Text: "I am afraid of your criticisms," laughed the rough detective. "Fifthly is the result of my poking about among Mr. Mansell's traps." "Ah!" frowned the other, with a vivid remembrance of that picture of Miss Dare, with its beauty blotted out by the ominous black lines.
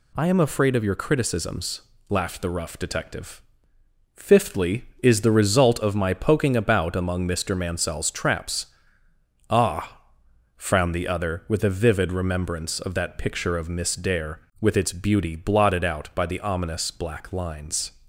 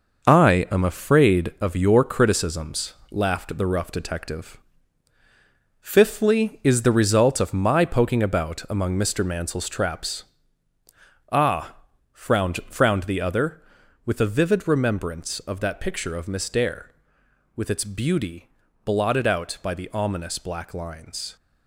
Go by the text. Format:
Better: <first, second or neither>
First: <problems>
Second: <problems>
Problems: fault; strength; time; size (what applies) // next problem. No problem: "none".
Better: first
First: none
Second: says "frowned" twice; at 12.6 s // pauses between "beauty" and "blotted"; at 18.4 s; 0.38 s long